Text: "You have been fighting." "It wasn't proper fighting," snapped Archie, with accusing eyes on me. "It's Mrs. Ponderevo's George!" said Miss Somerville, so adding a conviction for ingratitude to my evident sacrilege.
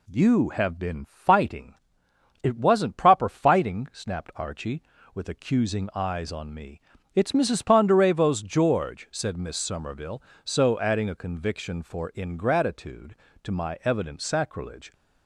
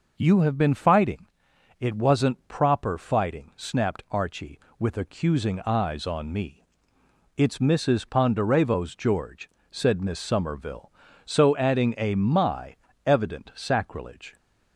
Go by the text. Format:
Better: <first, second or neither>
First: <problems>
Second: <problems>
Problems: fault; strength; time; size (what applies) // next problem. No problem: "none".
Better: first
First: none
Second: skips "conviction for ingratitude to"; at 12.1 s // pauses between "my" and "evident"; slight; at 12.7 s; 0.28 s long